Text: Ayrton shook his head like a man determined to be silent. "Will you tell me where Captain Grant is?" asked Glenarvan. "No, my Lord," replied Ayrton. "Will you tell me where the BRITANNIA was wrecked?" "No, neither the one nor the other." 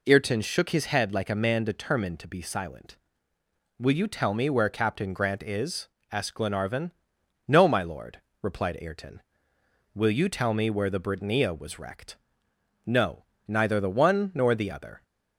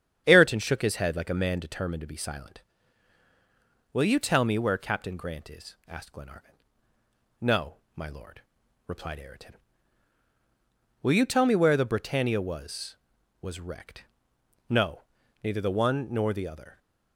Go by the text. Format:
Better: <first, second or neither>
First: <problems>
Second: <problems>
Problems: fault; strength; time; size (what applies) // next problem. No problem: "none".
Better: first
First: none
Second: starts louder than the rest; strong; until 1.2 s; 8.5 dB // says "was" twice; at 13.4 s